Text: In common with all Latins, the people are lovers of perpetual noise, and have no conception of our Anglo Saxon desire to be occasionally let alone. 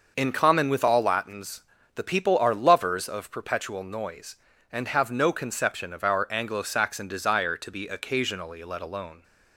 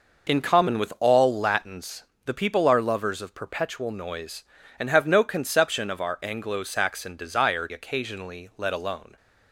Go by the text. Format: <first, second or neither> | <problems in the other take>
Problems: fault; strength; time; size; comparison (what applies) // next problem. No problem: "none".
first | skips "to be"; at 7.6 s